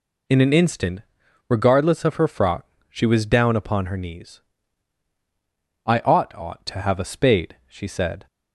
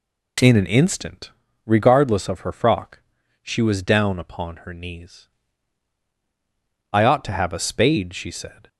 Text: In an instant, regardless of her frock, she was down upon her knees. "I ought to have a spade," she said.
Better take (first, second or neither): second